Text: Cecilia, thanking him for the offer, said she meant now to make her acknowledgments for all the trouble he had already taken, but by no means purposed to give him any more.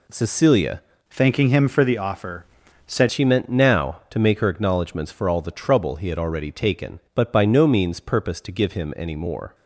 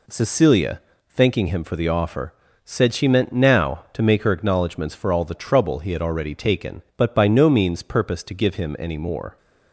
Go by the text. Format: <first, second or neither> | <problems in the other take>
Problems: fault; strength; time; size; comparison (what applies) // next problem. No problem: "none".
second | changes voice from "thanking" to "said"; from 1.1 to 3.0 s; 1.9 s long